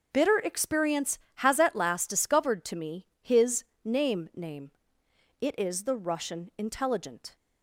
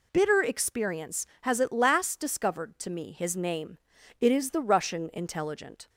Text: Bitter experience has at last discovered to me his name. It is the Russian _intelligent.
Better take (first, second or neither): second